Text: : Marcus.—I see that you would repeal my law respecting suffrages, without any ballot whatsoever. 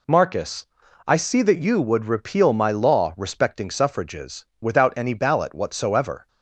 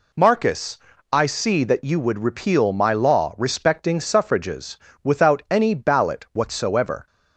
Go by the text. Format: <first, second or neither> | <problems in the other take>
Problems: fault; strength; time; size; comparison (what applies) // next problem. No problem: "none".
neither | none